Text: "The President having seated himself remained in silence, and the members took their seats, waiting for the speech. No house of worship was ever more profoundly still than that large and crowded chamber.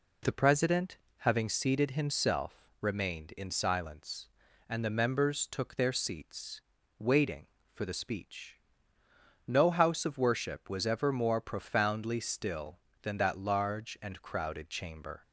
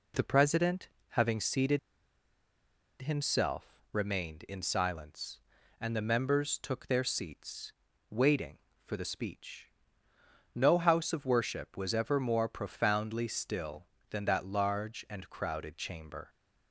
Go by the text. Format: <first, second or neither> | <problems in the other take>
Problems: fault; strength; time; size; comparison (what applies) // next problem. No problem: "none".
first | pauses between "President" and "having"; slight; at 0.8 s; 0.22 s long; slight in the first // pauses between "seated" and "himself"; at 1.7 s; 1.2 s long